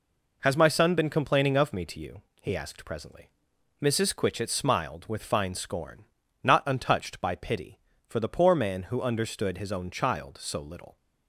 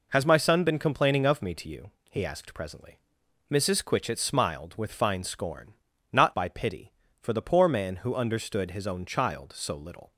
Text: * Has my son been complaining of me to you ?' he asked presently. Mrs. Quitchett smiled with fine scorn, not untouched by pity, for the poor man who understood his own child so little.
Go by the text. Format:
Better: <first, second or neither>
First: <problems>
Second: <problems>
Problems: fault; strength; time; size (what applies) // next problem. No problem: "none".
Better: first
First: none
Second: skips "untouched"; at 6.3 s